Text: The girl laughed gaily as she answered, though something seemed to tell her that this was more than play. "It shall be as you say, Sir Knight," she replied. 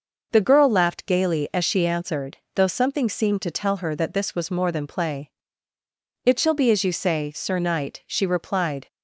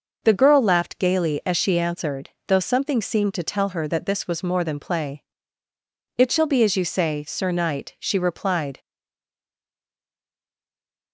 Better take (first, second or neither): first